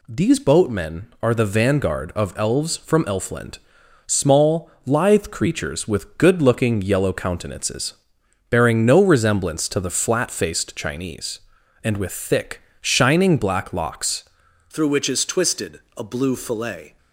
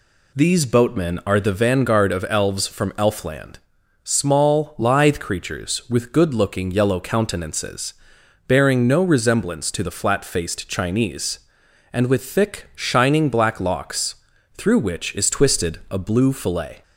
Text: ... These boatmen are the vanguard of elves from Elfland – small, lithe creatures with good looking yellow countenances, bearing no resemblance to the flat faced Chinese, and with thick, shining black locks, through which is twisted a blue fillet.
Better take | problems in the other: second | changes voice at "through"; from 14.7 s on; 2.2 s long // pauses between "twisted" and "a"; slight; at 15.7 s; 0.16 s long

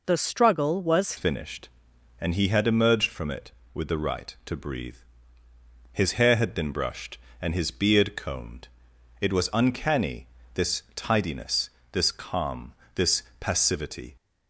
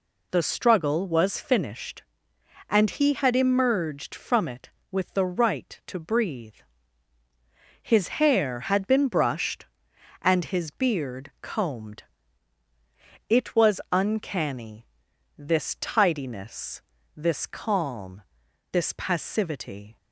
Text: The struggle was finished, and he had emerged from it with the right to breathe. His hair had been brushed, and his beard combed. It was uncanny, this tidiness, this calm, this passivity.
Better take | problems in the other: second | changes voice at "finished"; from 1.1 s on; 13.0 s long // pauses between "this" and "passivity"; slight; at 13.2 s; 0.16 s long

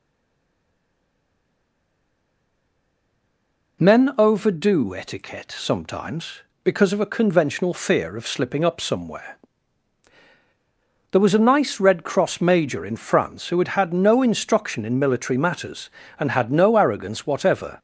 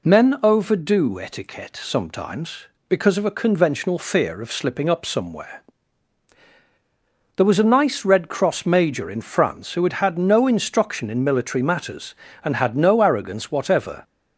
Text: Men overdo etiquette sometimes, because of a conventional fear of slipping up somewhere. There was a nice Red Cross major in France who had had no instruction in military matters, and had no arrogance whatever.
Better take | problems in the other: second | stays silent before the first word; strong; until 3.8 s; 3.8 s long

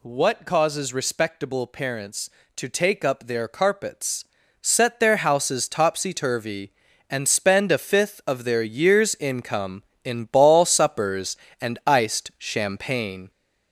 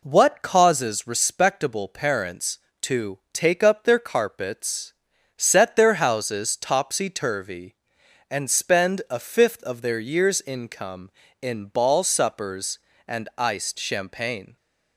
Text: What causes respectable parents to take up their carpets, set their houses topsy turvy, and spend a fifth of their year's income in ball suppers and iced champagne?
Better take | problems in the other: second | gets louder; throughout; 3.5 dB

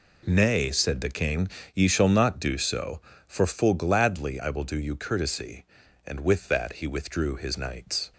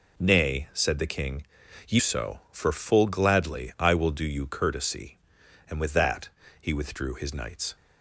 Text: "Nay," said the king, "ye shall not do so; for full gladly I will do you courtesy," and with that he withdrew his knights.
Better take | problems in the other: first | skips "shall not do"; at 1.9 s // pauses between "that" and "he"; slight; at 6.2 s; 0.30 s long

